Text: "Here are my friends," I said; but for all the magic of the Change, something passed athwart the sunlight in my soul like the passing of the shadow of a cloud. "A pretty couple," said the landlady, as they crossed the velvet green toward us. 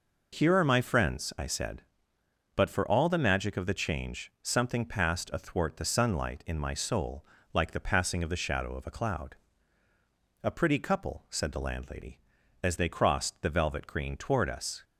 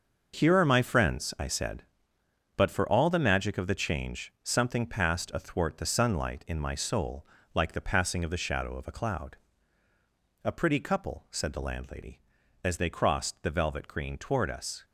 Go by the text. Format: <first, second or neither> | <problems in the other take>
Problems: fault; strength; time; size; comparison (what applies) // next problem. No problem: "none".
first | gets quieter; strong; throughout; 9.5 dB // pauses between "soul" and "like"; slight; at 7.2 s; 0.30 s long; slight in the first